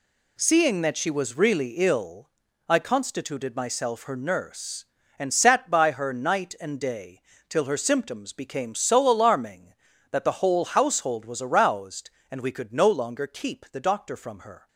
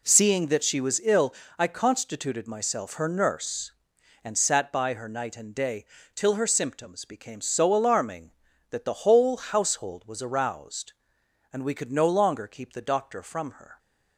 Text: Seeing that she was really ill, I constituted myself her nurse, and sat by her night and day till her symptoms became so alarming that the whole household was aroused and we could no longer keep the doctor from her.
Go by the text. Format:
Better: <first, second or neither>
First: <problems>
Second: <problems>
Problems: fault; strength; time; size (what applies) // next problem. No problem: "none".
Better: first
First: pauses between "day" and "till"; slight; at 7.2 s; 0.28 s long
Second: skips "really"; at 1.0 s // pauses between "day" and "till"; slight; at 5.8 s; 0.28 s long